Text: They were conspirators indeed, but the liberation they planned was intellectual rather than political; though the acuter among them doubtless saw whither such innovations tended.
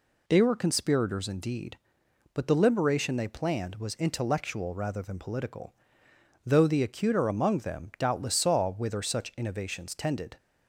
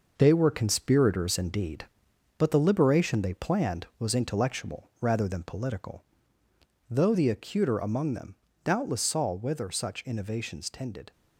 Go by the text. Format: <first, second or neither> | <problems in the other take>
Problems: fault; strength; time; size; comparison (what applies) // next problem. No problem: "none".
first | gets quieter; throughout; 7 dB // pauses between "them" and "doubtless"; slight; at 8.3 s; 0.28 s long